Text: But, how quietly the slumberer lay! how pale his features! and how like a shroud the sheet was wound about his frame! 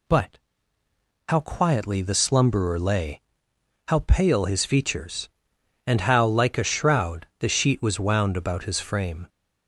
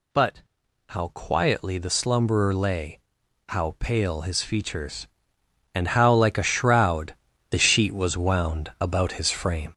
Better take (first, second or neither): first